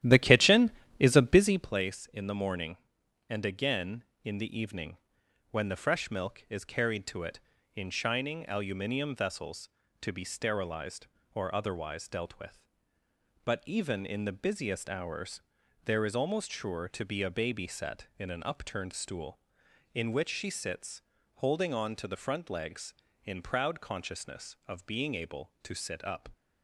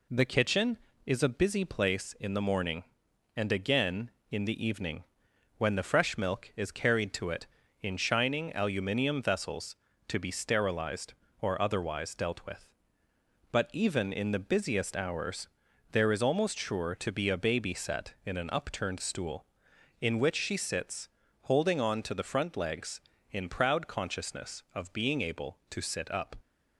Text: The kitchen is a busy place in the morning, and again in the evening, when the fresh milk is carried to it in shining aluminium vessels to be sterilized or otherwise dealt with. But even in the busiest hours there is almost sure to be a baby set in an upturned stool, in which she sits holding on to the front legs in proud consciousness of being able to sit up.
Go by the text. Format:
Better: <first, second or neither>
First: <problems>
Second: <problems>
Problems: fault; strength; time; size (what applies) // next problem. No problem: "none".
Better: second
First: starts louder than the rest; strong; until 1.7 s; 12.5 dB // pauses between "hours" and "there"; noticeable; at 15.3 s; 0.46 s long // pauses between "sits" and "holding"; slight; at 21.0 s; 0.32 s long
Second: pauses between "hours" and "there"; noticeable; at 15.4 s; 0.46 s long // pauses between "sits" and "holding"; slight; at 21.1 s; 0.32 s long